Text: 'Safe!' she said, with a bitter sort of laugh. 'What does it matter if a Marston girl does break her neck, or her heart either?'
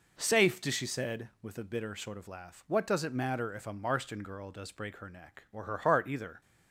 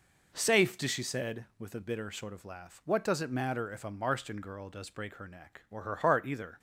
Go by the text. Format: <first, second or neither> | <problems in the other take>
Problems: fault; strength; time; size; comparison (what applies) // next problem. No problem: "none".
neither | none